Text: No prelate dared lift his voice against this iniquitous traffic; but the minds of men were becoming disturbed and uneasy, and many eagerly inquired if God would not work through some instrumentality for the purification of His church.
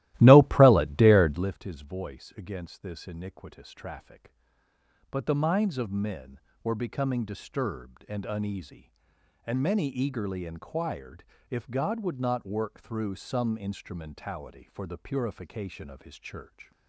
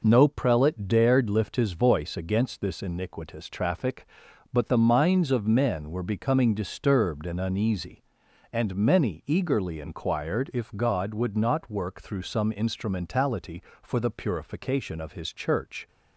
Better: second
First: starts louder than the rest; strong; until 1.6 s; 15.5 dB // pauses between "inquired" and "if"; slight; at 11.2 s; 0.24 s long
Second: none

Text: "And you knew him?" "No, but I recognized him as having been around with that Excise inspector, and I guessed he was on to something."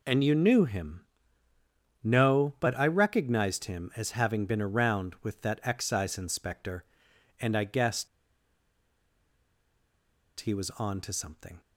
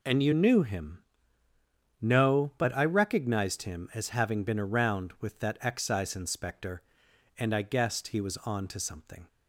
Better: second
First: pauses between "guessed" and "he"; strong; at 8.0 s; 2.3 s long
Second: none

